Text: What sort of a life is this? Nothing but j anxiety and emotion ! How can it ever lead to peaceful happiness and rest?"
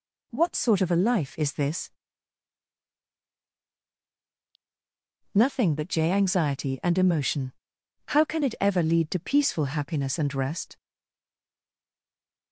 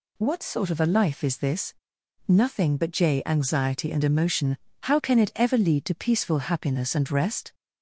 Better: second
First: stays silent after the last word; noticeable; from 10.7 s on; 1.8 s long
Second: none

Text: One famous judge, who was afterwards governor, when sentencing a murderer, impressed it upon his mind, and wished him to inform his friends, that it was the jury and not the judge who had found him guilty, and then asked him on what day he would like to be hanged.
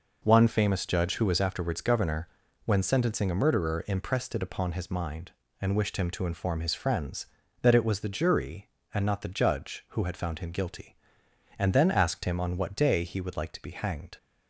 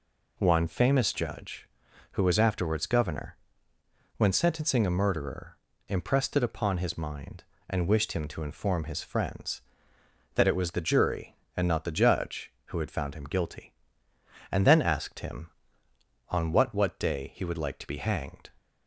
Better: first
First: none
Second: says "what" twice; at 16.7 s

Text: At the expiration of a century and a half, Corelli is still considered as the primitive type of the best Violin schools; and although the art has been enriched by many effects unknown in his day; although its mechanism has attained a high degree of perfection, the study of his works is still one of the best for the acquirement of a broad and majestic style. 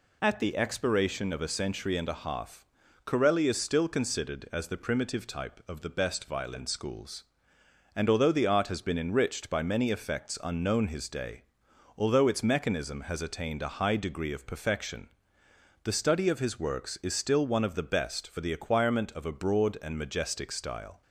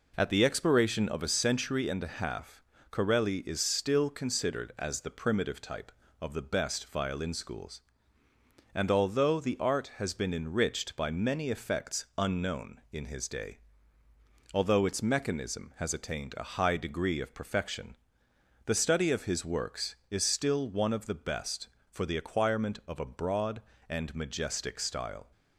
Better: second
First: skips "in"; at 10.8 s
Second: none

